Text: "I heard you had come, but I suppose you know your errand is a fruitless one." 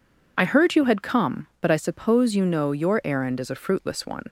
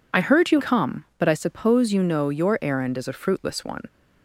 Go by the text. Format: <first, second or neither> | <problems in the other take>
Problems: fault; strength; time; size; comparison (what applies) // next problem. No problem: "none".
first | skips "had"; at 0.6 s